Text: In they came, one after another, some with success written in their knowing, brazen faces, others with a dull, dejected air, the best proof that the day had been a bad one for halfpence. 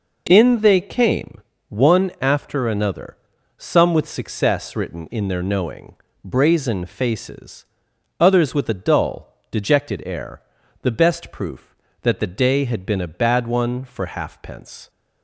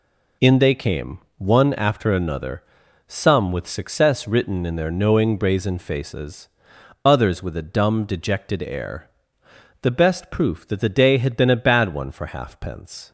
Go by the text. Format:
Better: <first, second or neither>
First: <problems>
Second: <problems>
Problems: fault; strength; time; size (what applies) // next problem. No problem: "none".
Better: first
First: none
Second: says "dumb" for "dull"; at 7.6 s